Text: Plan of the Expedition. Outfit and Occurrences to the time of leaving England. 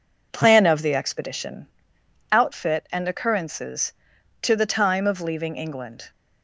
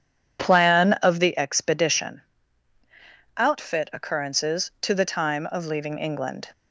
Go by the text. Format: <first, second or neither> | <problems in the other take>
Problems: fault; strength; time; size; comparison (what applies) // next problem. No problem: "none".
first | skips "and"; at 3.9 s